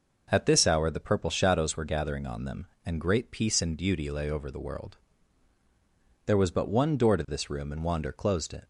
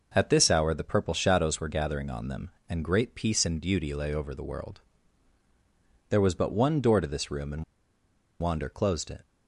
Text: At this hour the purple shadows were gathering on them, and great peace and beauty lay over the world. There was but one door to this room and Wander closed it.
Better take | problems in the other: first | pauses between "and" and "Wander"; noticeable; at 7.6 s; 0.76 s long

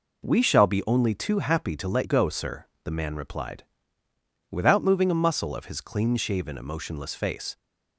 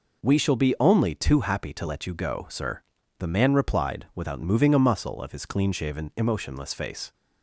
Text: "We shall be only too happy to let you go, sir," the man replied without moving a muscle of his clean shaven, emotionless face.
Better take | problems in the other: second | skips "you"; at 2.0 s // pauses between "replied" and "without"; noticeable; at 3.6 s; 0.86 s long

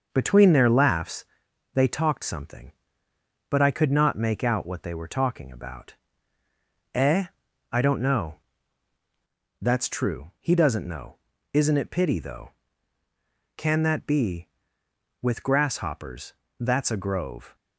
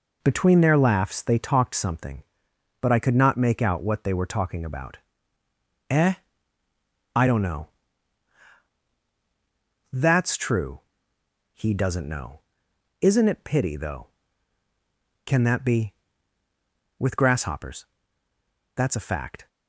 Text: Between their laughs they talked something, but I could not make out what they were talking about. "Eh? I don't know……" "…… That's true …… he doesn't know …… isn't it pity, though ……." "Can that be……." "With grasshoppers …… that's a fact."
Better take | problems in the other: second | starts louder than the rest; until 1.1 s; 6.5 dB // pauses between "laughs" and "they"; noticeable; at 1.2 s; 0.50 s long // says "grove" for "fact"; at 16.9 s

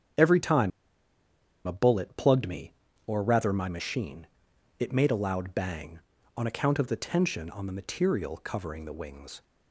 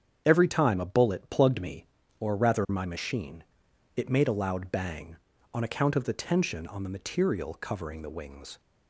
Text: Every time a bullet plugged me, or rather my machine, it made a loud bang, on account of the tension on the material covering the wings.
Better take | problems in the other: second | starts louder than the rest; strong; until 2.1 s; 8 dB; strong in the second // pauses between "time" and "a"; noticeable; at 0.7 s; 0.96 s long

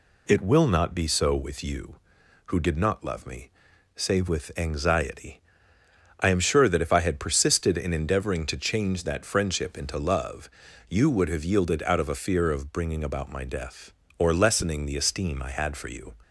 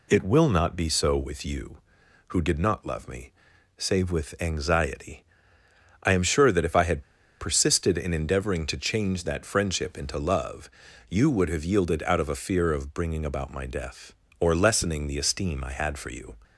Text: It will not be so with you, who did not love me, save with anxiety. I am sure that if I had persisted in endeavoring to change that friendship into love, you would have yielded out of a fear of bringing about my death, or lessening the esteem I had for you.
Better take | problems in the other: first | pauses between "had" and "persisted"; at 7.0 s; 0.37 s long

